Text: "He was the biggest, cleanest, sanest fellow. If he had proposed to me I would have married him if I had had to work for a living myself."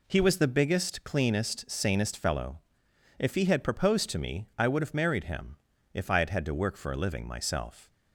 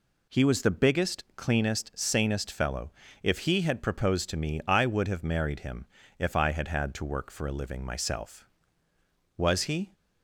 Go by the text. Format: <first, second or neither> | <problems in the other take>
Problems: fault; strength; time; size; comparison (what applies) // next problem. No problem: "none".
first | pauses between "him" and "if"; slight; at 5.8 s; 0.32 s long; slight in the first // goes on to say "Was he"; from 9.3 s on; 0.56 s long